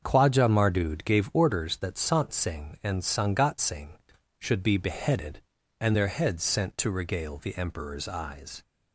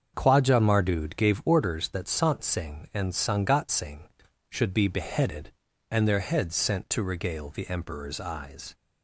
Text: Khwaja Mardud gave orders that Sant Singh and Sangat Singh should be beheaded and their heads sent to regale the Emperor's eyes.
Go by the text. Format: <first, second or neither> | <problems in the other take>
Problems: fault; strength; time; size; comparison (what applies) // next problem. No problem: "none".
neither | starts louder than the rest; the same in both